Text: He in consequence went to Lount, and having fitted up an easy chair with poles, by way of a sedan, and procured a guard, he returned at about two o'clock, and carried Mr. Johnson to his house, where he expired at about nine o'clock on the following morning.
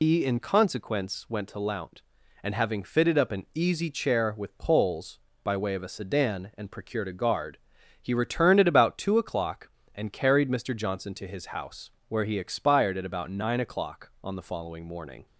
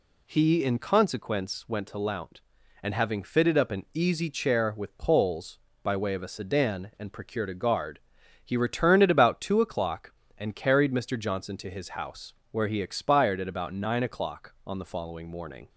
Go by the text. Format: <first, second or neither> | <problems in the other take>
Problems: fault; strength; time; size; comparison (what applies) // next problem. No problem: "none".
second | loses the start of "He"; at 0.0 s; 155 ms